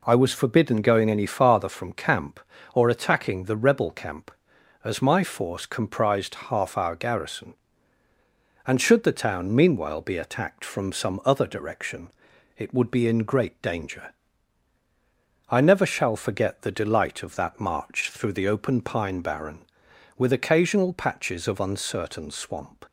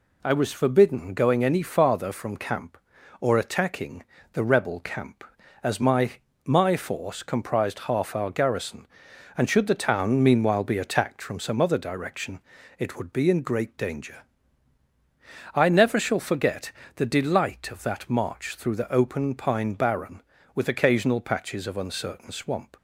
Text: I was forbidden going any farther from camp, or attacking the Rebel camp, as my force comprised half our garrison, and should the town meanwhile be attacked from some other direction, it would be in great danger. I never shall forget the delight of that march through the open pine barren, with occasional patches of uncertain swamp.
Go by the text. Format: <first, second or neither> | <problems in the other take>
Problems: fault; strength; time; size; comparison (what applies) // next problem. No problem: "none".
first | pauses between "attacking" and "the"; slight; at 4.0 s; 0.32 s long // says "my" twice; at 6.4 s // pauses between "forget" and "the"; slight; at 16.7 s; 0.26 s long